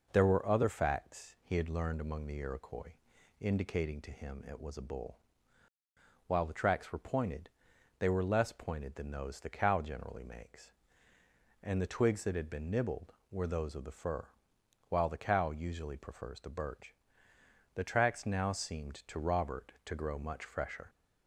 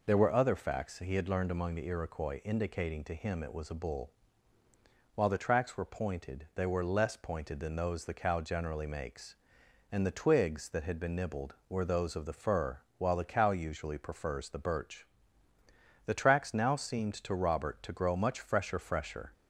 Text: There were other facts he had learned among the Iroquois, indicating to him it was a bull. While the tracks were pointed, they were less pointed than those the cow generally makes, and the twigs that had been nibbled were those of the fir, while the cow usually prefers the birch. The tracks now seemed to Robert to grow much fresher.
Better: first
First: none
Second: says "fresher" twice; at 18.7 s

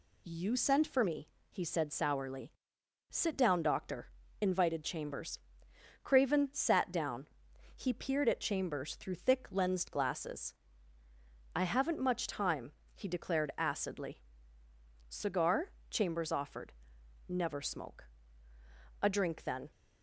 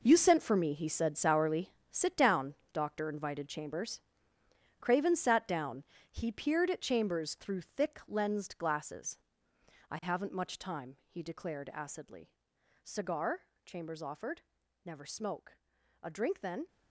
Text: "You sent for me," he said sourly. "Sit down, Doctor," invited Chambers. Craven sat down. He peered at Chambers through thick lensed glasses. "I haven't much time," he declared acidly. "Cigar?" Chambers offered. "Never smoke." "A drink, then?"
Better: first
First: none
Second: gets quieter; strong; throughout; 11.5 dB

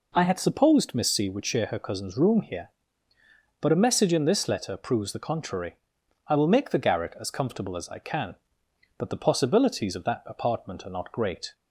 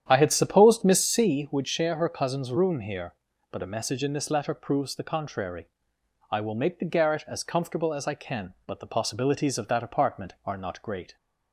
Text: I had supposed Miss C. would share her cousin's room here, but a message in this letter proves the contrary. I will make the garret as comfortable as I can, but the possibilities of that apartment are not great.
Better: first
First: none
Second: starts louder than the rest; strong; until 1.4 s; 9.5 dB

